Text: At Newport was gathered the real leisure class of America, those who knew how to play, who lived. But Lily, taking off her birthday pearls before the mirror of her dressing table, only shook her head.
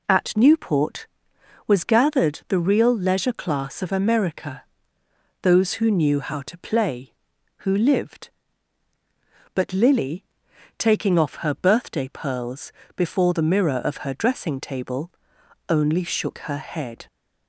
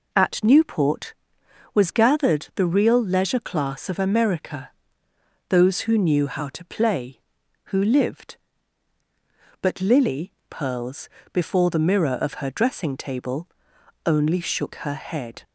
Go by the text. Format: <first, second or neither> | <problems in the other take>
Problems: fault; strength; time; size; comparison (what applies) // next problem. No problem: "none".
first | skips "taking off her birthday"; at 10.4 s // pauses between "pearls" and "before"; slight; at 11.1 s; 0.24 s long; slight in the first